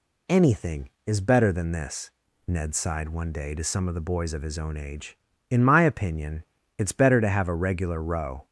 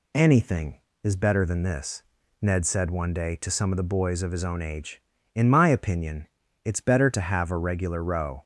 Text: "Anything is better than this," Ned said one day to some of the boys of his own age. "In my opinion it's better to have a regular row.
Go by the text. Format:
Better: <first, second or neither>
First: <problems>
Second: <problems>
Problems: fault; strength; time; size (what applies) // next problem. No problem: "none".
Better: second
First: says "sighed" for "said"; at 2.7 s // pauses between "opinion" and "it's"; slight; at 6.4 s; 0.36 s long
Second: pauses between "opinion" and "it's"; at 6.2 s; 0.38 s long